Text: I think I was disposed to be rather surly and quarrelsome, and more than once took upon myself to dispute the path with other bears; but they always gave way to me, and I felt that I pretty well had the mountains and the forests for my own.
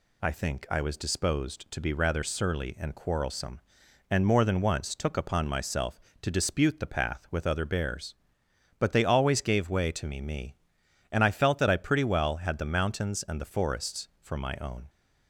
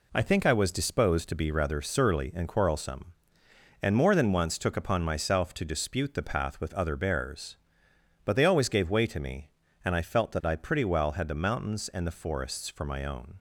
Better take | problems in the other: second | says "me" twice; at 10.1 s

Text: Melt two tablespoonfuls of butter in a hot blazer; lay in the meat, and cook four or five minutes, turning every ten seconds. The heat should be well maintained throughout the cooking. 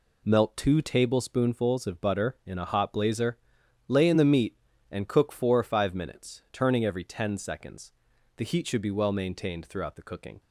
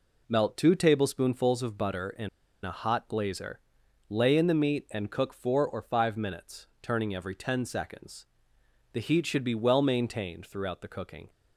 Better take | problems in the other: first | pauses between "in" and "a"; slight; at 2.2 s; 0.36 s long

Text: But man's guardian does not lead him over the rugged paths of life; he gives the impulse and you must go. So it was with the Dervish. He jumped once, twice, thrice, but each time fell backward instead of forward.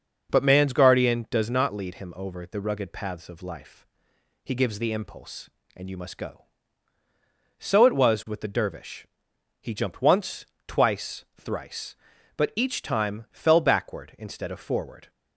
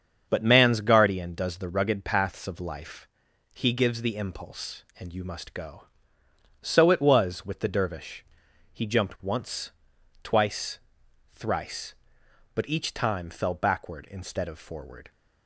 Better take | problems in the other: first | starts louder than the rest; strong; until 1.3 s; 7 dB // skips "not lead him over"; at 1.5 s

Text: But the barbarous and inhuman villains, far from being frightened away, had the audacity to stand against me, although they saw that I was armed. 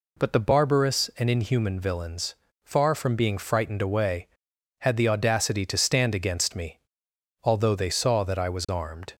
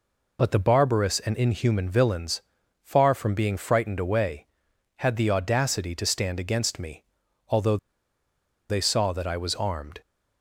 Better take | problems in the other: first | pauses between "although" and "they"; noticeable; at 7.7 s; 0.93 s long

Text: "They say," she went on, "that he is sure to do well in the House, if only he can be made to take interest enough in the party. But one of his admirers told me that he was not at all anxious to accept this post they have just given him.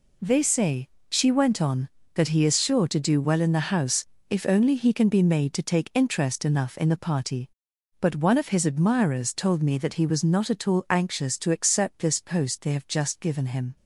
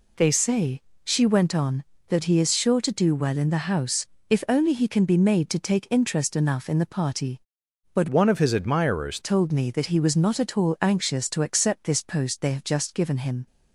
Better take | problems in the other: first | changes voice from "one" to "admirers"; from 8.0 to 9.1 s; 1.1 s long

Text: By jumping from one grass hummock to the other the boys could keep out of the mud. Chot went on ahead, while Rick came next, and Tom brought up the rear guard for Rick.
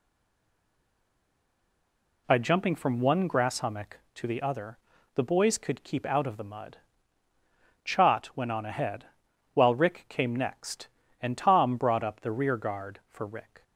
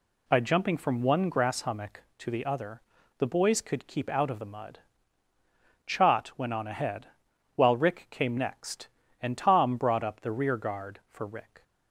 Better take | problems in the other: second | stays silent before the first word; until 2.2 s; 2.2 s long // pauses between "other" and "the"; at 4.7 s; 0.38 s long; also in the second

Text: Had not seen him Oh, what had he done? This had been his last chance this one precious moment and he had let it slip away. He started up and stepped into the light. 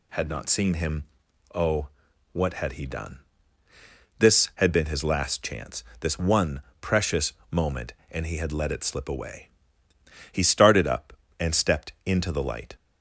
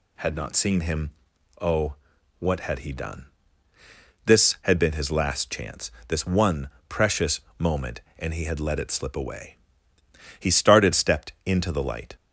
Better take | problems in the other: first | pauses between "him" and "Oh"; noticeable; at 1.1 s; 0.48 s long; noticeable in the first // pauses between "chance" and "this"; slight; at 5.9 s; 0.16 s long; slight in the first // pauses between "one" and "precious"; slight; at 6.6 s; 0.20 s long; slight in the first // pauses between "precious" and "moment"; slight; at 7.4 s; 0.18 s long; slight in the first // skips "up and"; at 10.9 s

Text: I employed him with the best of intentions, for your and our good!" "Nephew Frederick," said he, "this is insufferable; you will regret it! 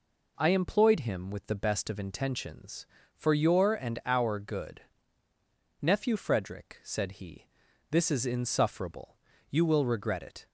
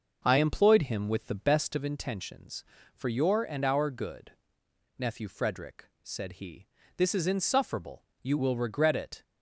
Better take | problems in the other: first | starts louder than the rest; noticeable; until 1.9 s; 6 dB

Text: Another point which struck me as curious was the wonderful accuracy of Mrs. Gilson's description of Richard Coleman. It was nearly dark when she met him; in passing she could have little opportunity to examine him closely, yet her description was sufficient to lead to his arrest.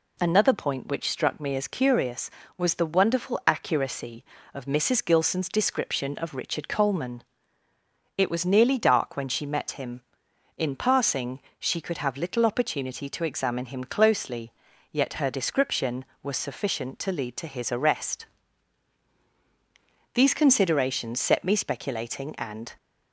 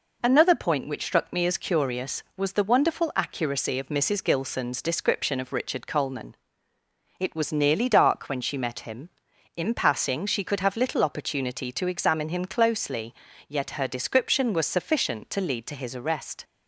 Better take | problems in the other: second | pauses between "passing" and "she"; slight; at 11.3 s; 0.22 s long // goes on to say "These considerations set me speculating and"; strong; from 20.1 s on; 2.5 s long

